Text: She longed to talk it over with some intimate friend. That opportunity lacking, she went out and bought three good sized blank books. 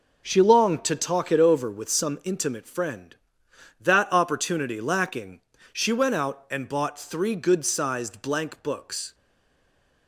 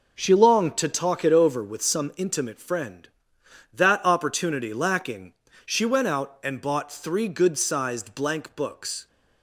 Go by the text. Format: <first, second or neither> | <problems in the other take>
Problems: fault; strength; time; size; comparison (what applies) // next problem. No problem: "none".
second | stays silent after the last word; slight; from 9.1 s on; 0.9 s long